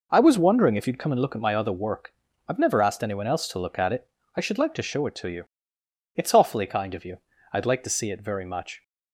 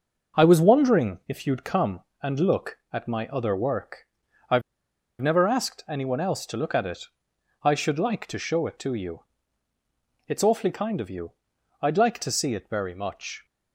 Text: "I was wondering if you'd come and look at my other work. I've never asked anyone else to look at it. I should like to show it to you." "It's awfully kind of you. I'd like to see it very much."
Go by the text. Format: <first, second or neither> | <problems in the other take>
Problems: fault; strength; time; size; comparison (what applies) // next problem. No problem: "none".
first | starts louder than the rest; noticeable; until 1.4 s; 6 dB // pauses between "I've" and "never"; noticeable; at 4.6 s; 0.59 s long